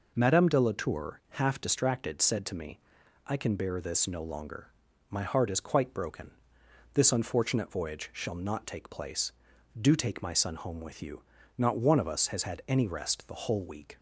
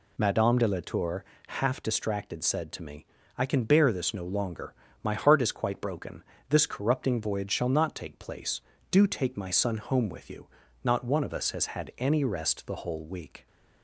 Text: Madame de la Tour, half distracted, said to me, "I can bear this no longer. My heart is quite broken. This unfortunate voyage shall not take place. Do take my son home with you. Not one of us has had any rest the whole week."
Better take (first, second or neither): first